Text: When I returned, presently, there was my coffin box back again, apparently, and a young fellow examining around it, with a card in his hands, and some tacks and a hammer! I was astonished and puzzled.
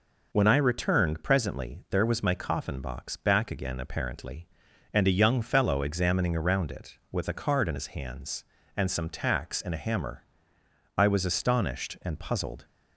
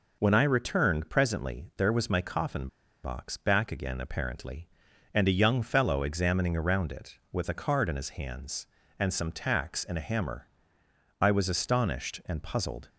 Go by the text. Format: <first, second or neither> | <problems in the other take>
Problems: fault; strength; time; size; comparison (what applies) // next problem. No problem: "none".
first | pauses between "coffin" and "box"; slight; at 2.6 s; 0.35 s long